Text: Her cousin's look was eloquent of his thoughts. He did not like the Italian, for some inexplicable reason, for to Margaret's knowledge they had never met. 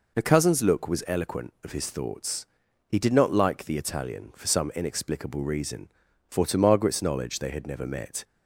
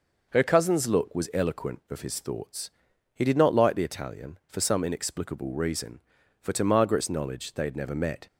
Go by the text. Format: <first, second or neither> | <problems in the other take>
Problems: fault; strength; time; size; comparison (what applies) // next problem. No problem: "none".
neither | none